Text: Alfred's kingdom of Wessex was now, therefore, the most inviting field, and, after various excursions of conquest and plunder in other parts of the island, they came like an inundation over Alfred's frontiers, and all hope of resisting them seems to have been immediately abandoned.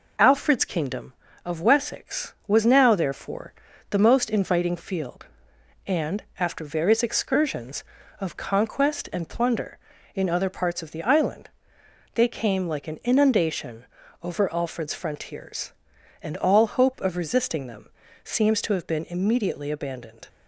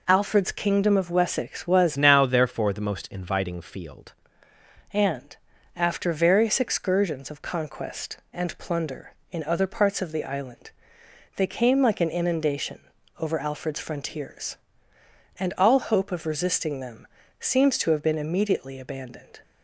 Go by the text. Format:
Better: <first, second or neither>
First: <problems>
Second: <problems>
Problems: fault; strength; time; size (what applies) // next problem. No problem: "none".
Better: first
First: pauses between "inundation" and "over"; at 13.8 s; 0.38 s long // pauses between "them" and "seems"; slight; at 17.8 s; 0.34 s long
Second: changes voice from "now" to "field"; from 1.9 to 4.1 s; 2.2 s long // pauses between "inundation" and "over"; at 12.7 s; 0.40 s long // pauses between "them" and "seems"; slight; at 17.0 s; 0.34 s long